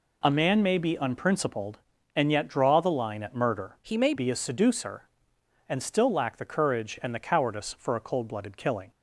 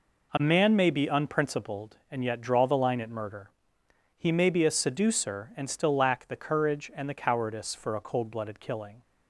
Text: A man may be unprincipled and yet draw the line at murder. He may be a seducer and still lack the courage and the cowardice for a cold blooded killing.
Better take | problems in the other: second | changes voice from "He" to "may"; from 3.8 to 4.1 s; 0.3 s long

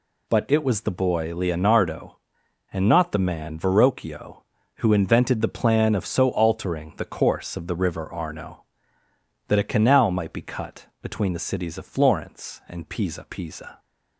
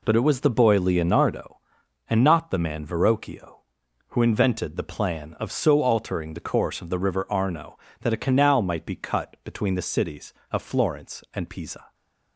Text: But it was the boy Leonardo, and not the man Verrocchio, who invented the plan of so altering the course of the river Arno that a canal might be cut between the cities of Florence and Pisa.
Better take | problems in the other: second | pauses between "cut" and "between"; slight; at 10.8 s; 0.16 s long // says "Pisa" twice; at 13.2 s

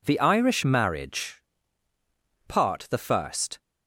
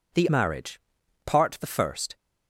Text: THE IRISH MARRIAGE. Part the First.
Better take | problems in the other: first | skips "IRISH"; at 0.2 s

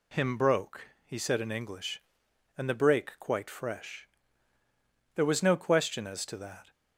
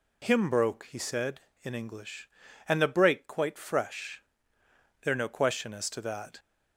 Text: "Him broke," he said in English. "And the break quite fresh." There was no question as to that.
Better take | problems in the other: first | skips "was"; at 5.1 s

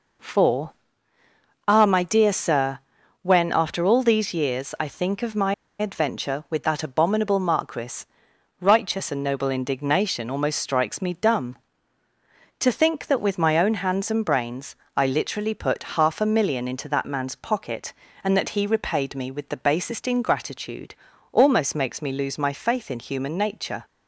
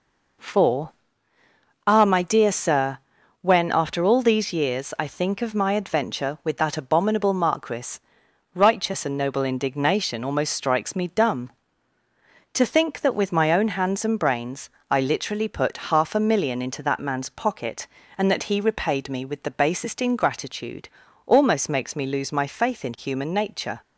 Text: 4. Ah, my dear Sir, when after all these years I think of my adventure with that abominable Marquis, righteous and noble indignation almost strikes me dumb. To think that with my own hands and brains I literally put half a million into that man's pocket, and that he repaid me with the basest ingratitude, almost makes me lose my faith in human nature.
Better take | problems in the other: second | pauses between "my" and "adventure"; slight; at 5.5 s; 0.25 s long // pauses between "brains" and "I"; slight; at 14.7 s; 0.20 s long; slight in the second

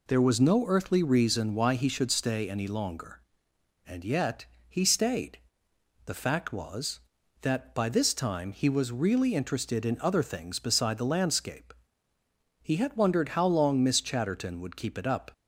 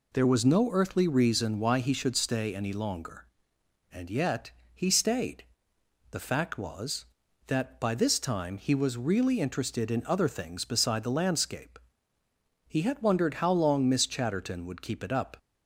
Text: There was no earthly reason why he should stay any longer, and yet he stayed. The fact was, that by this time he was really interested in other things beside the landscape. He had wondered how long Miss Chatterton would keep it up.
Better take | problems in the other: neither | pauses between "yet" and "he"; slight; the same in both

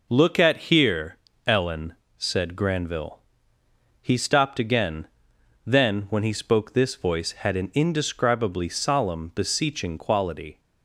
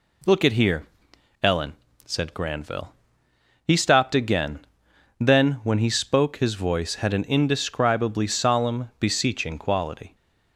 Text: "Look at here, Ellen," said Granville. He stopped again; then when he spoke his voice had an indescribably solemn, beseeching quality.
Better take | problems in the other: second | says "this" for "his"; at 6.7 s

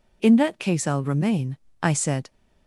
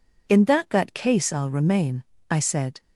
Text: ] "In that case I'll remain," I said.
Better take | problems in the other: first | says "that" twice; at 0.6 s

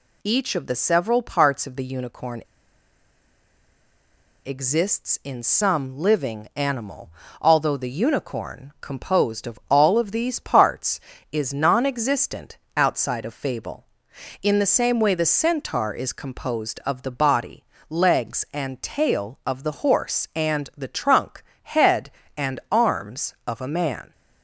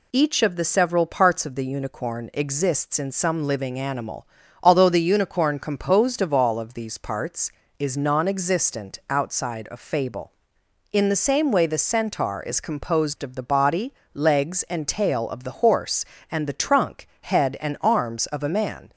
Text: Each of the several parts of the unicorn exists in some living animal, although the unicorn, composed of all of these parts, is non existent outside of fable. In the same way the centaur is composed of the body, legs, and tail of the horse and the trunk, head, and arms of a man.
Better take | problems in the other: second | pauses between "unicorn" and "exists"; strong; at 2.4 s; 2.0 s long // pauses between "existent" and "outside"; slight; at 12.5 s; 0.18 s long

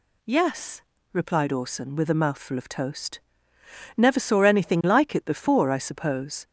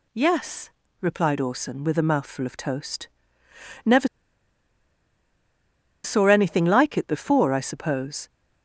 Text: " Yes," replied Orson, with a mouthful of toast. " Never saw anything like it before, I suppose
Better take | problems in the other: first | pauses between "Never" and "saw"; strong; at 4.0 s; 1.9 s long

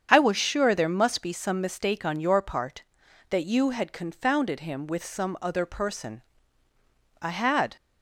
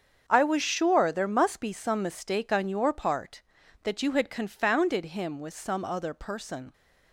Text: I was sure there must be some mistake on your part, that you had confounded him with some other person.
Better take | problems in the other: second | starts louder than the rest; strong; until 1.1 s; 7.5 dB; strong in the second // goes on to say "I had"; from 7.2 s on; 0.54 s long

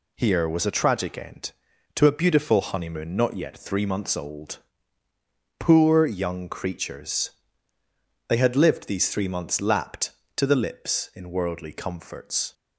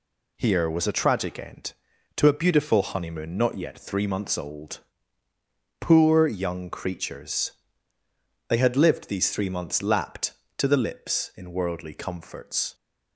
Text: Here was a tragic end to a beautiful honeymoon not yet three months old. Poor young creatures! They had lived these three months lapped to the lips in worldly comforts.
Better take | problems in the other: neither | none

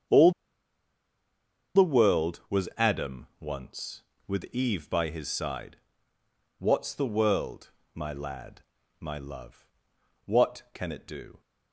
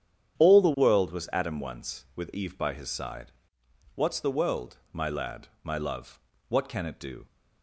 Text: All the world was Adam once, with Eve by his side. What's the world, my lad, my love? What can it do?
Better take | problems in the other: second | starts louder than the rest; strong; until 2.6 s; 7.5 dB; strong in the second // pauses between "All" and "the"; strong; at 0.3 s; 1.4 s long

